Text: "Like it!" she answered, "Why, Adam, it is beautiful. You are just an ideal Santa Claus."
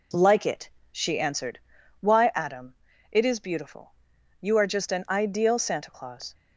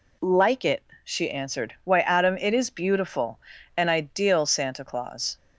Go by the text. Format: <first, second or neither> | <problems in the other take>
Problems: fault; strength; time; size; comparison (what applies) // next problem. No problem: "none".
first | skips "You are just"; at 3.5 s